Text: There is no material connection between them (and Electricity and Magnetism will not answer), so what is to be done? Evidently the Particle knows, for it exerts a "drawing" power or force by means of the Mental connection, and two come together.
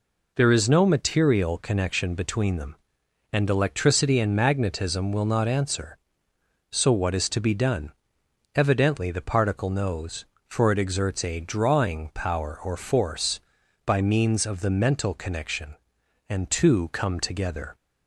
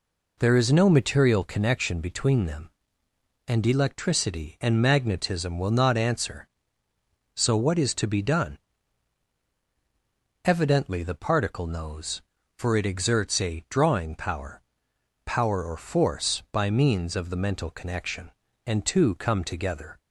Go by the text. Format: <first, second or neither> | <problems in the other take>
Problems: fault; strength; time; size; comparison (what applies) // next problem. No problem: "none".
first | says "power" twice; at 15.2 s